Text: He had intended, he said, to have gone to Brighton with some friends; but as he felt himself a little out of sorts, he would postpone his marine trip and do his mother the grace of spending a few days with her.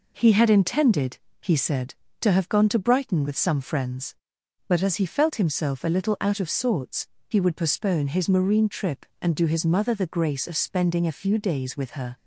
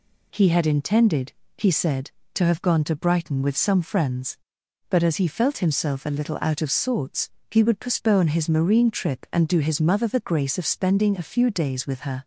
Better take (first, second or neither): neither